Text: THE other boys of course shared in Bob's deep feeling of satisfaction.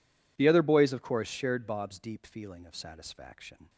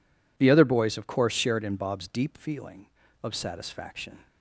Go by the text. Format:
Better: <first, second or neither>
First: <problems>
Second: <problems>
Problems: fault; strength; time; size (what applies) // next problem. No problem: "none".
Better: second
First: skips "in"; at 1.6 s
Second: none